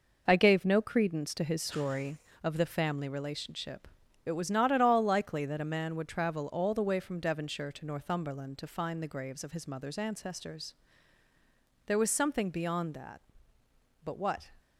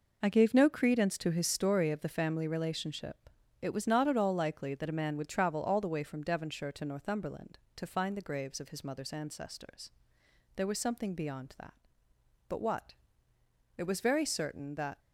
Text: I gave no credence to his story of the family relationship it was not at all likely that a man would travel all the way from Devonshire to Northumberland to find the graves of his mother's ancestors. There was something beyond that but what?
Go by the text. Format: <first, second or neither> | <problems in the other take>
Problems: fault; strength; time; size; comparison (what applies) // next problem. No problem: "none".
first | pauses between "relationship" and "it"; slight; at 3.2 s; 0.32 s long; also in the first // goes on to say "It was very certain that"; noticeable; from 13.7 s on; 1.2 s long